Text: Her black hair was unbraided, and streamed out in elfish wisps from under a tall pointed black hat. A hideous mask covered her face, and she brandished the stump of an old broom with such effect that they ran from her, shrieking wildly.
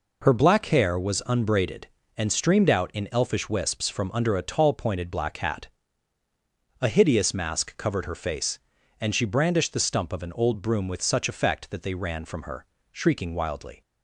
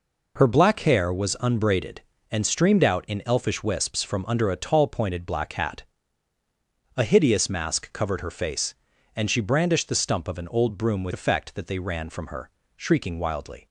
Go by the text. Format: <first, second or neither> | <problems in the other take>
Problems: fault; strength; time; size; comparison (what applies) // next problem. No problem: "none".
first | skips "such"; at 11.1 s